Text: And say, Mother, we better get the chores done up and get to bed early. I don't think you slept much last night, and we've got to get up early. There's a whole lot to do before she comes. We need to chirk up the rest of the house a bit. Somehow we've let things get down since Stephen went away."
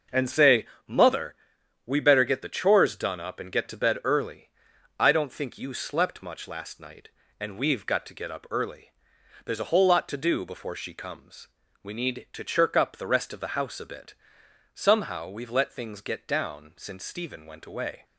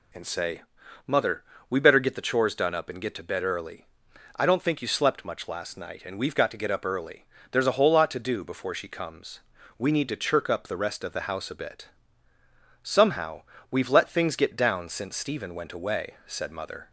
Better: first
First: none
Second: pauses between "Somehow" and "we've"; slight; at 13.4 s; 0.28 s long // goes on to say "Said Mother"; noticeable; from 16.2 s on; 0.64 s long

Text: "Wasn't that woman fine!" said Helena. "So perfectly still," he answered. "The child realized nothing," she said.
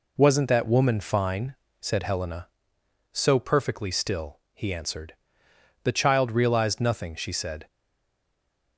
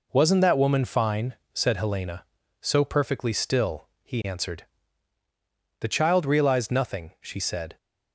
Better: second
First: stays silent after the last word; from 7.6 s on; 1.1 s long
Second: none

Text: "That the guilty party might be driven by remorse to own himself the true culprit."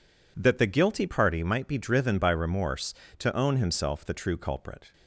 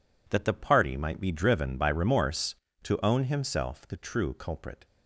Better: first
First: none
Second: skips "guilty"; at 0.5 s

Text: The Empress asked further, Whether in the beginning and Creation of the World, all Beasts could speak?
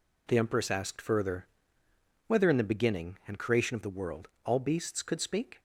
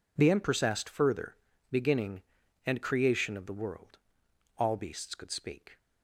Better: first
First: none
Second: skips "Whether in the"; at 1.5 s

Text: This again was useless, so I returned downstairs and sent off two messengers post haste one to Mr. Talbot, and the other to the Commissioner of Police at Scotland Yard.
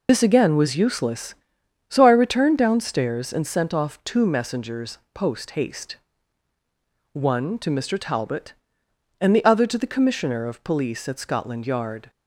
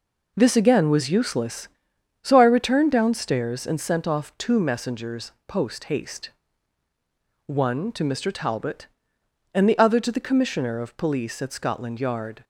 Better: second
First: loses the start of "This"; at 0.0 s; 75 ms // pauses between "messengers" and "post"; slight; at 4.9 s; 0.16 s long // pauses between "haste" and "one"; at 5.9 s; 1.1 s long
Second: pauses between "messengers" and "post"; slight; at 5.2 s; 0.16 s long // pauses between "haste" and "one"; at 6.2 s; 1.1 s long

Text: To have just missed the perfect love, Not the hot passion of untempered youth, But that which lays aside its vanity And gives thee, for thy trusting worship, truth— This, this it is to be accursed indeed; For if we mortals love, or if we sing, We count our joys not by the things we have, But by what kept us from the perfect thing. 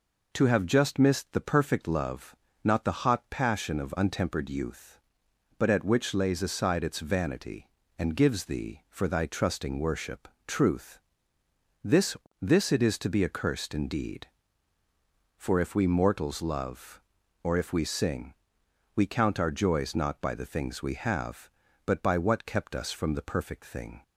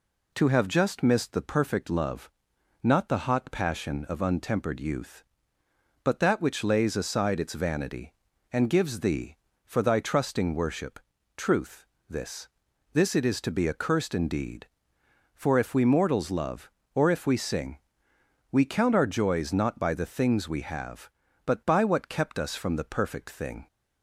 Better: second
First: says "at" for "that"; at 5.6 s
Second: none

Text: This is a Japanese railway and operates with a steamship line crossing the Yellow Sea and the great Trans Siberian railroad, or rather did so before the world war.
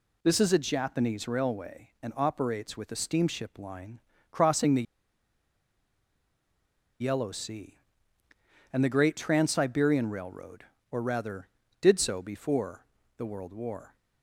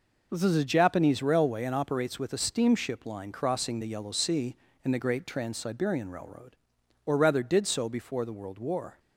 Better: second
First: pauses between "line" and "crossing"; slight; at 4.0 s; 0.30 s long // pauses between "the" and "Yellow"; strong; at 4.8 s; 2.1 s long // pauses between "before" and "the"; slight; at 12.8 s; 0.32 s long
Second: none

